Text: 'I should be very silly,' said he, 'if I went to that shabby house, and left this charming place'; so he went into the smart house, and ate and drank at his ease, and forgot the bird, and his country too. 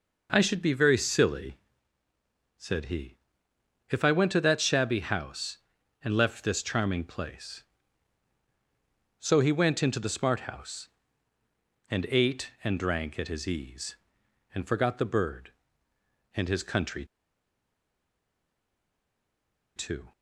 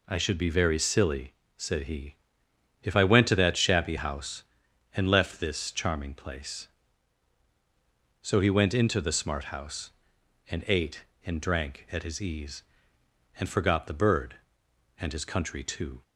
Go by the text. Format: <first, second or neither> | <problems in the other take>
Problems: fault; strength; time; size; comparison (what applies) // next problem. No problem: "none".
second | pauses between "country" and "too"; strong; at 17.0 s; 2.7 s long